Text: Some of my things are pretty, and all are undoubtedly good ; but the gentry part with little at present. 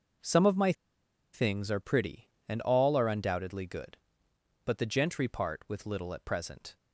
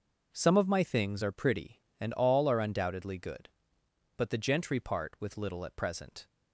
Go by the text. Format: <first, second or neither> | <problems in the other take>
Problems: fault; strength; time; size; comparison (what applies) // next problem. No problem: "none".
second | pauses between "my" and "things"; noticeable; at 0.7 s; 0.59 s long